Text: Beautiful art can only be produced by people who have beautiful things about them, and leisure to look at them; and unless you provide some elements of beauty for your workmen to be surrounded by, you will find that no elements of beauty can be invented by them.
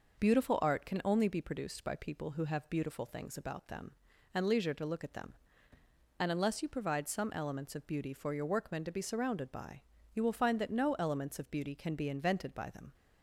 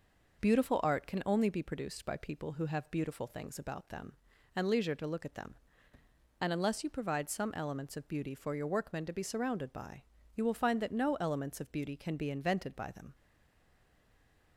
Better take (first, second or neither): first